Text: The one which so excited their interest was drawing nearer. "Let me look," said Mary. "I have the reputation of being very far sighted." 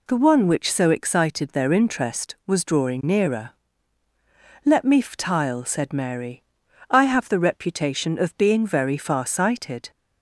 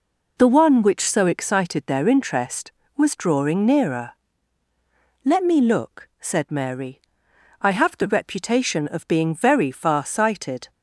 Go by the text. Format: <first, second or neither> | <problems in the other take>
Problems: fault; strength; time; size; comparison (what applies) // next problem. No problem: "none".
second | says "ftile" for "look"; at 5.0 s